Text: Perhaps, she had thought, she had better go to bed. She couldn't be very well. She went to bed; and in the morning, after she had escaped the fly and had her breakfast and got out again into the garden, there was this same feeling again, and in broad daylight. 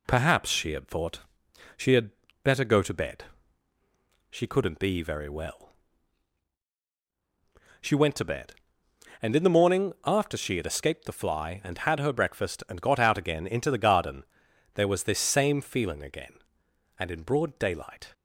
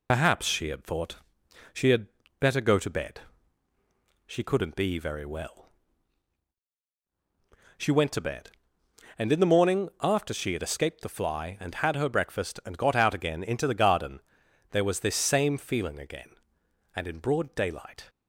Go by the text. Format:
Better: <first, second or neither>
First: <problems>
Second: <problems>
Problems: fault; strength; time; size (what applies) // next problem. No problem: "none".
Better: first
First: pauses between "had" and "better"; slight; at 2.1 s; 0.32 s long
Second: loses the start of "Perhaps"; at 0.0 s; 65 ms // pauses between "had" and "better"; slight; at 2.0 s; 0.32 s long